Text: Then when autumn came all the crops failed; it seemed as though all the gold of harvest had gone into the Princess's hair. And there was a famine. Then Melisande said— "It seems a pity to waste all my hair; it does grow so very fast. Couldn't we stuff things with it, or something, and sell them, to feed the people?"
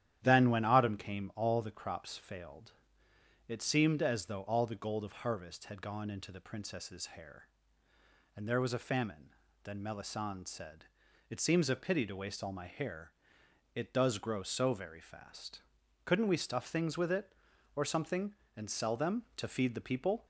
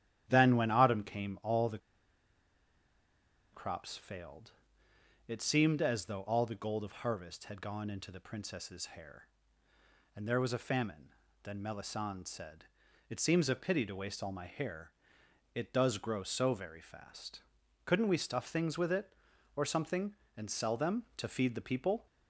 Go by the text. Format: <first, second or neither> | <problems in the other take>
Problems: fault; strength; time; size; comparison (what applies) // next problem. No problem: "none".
first | starts louder than the rest; strong; until 1.3 s; 11 dB; strong in the first // pauses between "the" and "crops"; strong; at 1.7 s; 1.7 s long